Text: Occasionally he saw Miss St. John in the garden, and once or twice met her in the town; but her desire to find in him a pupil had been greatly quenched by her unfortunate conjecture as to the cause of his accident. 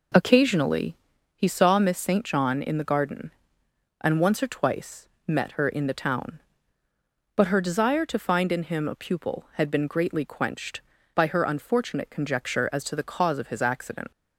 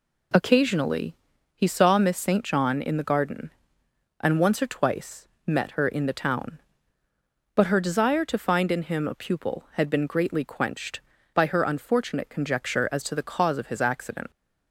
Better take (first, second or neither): second